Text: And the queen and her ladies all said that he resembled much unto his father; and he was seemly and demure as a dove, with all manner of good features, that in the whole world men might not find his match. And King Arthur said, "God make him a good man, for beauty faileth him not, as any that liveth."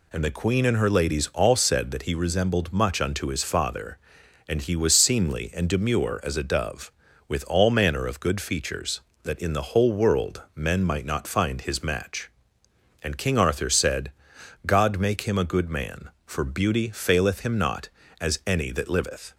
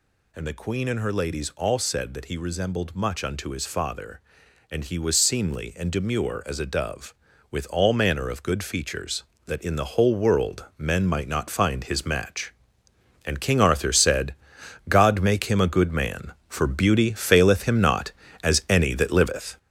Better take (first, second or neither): first